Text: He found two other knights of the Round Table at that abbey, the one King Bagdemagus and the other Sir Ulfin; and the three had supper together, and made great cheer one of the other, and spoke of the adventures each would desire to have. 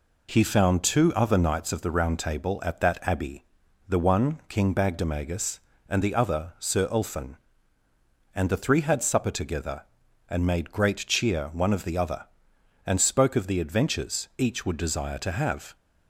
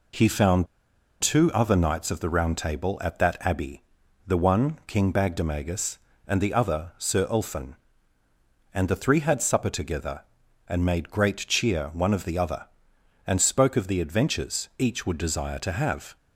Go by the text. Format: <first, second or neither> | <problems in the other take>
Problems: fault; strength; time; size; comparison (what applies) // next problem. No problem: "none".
first | pauses between "found" and "two"; noticeable; at 0.6 s; 0.55 s long